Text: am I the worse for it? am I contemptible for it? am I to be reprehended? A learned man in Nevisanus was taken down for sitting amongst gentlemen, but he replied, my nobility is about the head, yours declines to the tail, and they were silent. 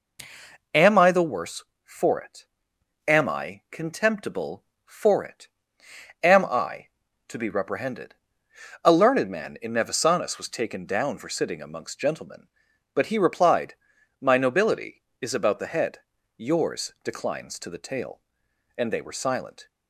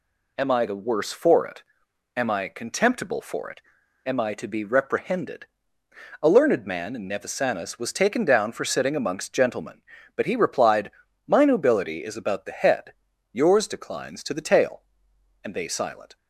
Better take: first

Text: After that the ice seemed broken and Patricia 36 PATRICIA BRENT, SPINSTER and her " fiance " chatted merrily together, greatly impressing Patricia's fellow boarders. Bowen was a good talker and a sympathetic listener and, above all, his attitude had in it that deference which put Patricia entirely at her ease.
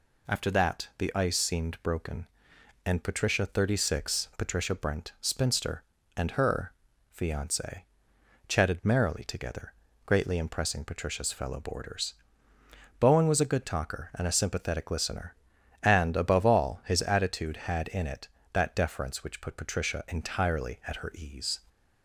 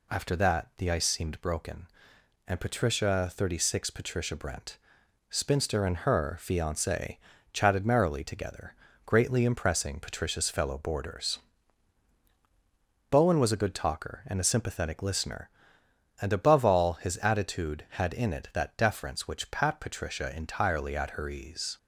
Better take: first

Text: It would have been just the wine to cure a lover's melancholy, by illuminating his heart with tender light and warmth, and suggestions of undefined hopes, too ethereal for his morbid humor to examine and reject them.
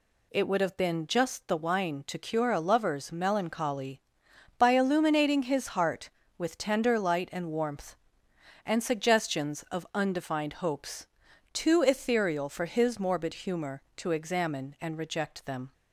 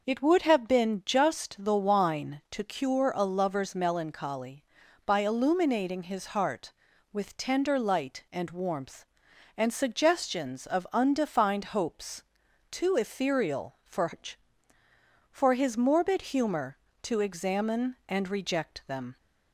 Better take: first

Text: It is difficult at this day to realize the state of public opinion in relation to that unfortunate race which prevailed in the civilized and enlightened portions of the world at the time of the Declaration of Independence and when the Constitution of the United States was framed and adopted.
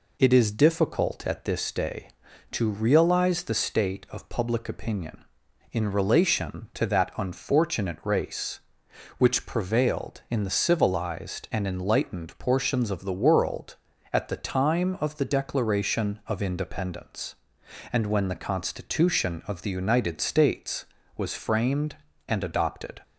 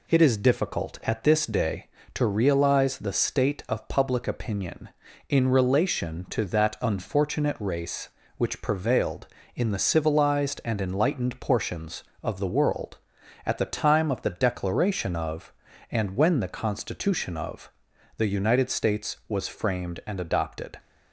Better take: first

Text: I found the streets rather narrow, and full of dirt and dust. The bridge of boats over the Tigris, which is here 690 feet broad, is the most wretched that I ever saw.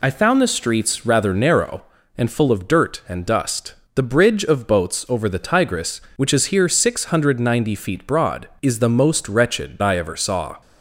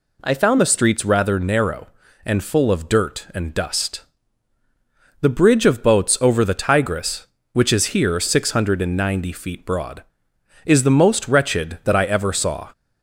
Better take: second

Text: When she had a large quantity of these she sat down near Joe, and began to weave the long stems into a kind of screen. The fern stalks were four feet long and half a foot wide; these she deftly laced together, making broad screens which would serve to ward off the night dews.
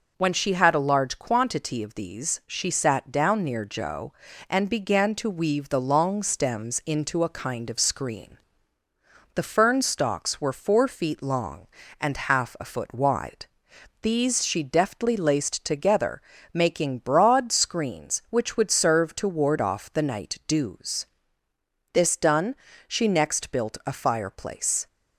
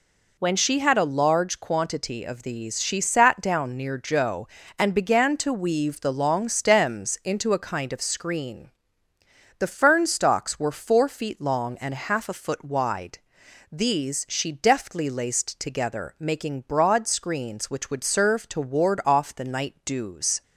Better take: second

